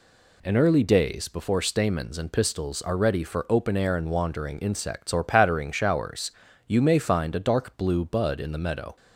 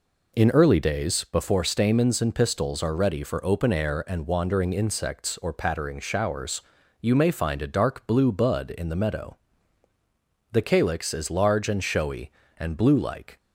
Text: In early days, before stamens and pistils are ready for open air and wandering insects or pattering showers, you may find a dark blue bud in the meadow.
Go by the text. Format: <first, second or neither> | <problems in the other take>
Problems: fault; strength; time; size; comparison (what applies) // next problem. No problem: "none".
first | goes on to say "The calyx is large and showy and blue like"; strong; from 10.5 s on; 2.8 s long